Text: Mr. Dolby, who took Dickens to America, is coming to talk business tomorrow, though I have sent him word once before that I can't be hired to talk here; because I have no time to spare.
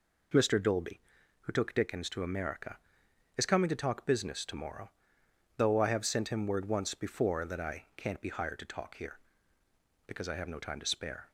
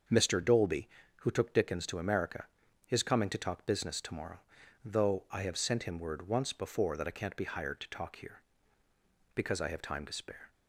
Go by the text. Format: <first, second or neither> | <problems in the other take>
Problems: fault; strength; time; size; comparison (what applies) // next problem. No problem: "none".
first | starts louder than the rest; until 1.4 s; 6.5 dB // skips "no"; at 9.8 s